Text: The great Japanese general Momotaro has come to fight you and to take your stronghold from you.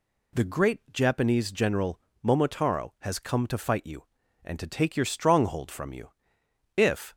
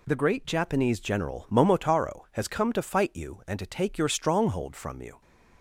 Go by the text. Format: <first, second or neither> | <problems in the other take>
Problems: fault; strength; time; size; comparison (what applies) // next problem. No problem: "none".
second | pauses between "general" and "Momotaro"; slight; at 2.0 s; 0.20 s long // goes on to say "If"; slight; from 6.7 s on; 0.38 s long